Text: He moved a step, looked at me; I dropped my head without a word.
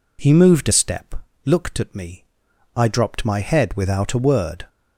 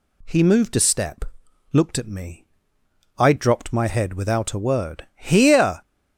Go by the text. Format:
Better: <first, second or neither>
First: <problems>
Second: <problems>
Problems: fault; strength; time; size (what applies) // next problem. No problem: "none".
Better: first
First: none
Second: goes on to say "Here"; noticeable; from 5.1 s on; 0.66 s long